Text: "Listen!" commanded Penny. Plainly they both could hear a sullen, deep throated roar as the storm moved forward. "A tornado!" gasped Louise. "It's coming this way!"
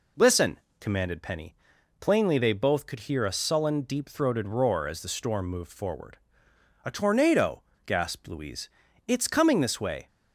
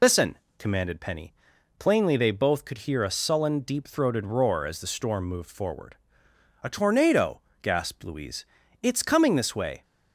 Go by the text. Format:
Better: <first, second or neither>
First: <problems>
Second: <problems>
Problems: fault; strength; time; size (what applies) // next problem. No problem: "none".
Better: first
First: none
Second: loses the start of "Listen"; at 0.0 s; 75 ms